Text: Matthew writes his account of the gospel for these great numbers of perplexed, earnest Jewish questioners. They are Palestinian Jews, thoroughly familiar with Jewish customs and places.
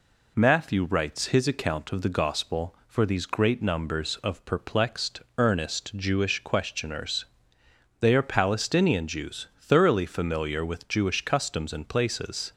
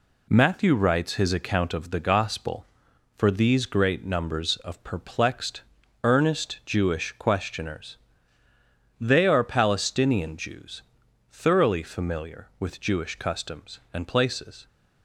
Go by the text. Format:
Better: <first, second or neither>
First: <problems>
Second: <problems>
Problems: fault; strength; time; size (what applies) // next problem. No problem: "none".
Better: neither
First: none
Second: none